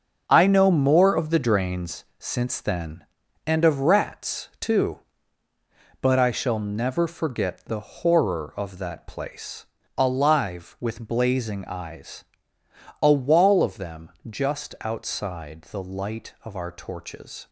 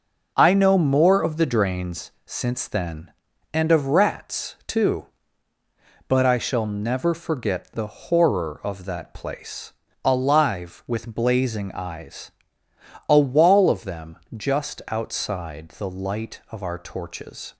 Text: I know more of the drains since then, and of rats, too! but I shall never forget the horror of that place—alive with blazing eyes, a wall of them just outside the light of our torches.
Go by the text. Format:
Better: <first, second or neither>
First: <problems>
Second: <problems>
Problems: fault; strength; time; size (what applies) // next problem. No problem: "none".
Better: second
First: gets quieter; strong; throughout; 9 dB // pauses between "them" and "just"; slight; at 14.1 s; 0.18 s long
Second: pauses between "them" and "just"; slight; at 14.1 s; 0.18 s long